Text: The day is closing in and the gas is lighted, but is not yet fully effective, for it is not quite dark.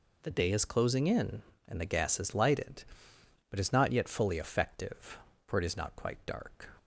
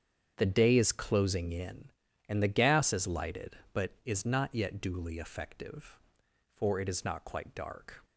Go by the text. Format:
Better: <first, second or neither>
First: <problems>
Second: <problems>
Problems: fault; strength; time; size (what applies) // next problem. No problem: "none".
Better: first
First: none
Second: starts louder than the rest; strong; until 1.3 s; 8 dB // says "duly" for "fully"; at 4.8 s